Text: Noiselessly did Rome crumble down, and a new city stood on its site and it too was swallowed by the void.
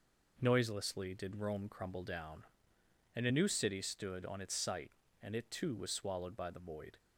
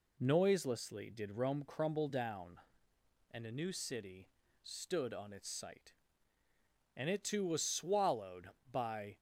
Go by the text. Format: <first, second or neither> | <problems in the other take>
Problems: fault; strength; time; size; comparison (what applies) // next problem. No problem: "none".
first | pauses between "city" and "stood"; slight; at 4.2 s; 0.34 s long // stops before "the void"; at 9.1 s